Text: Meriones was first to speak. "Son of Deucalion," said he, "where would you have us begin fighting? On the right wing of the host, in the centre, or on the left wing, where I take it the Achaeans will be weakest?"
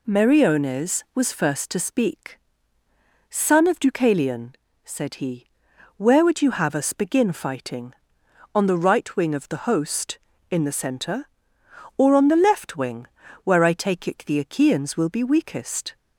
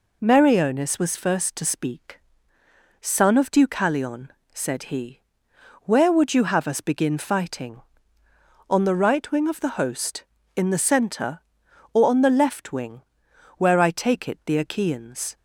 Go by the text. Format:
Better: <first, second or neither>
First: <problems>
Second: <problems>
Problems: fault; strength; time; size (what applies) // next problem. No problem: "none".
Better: first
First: none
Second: stops before "will be weakest"; at 15.3 s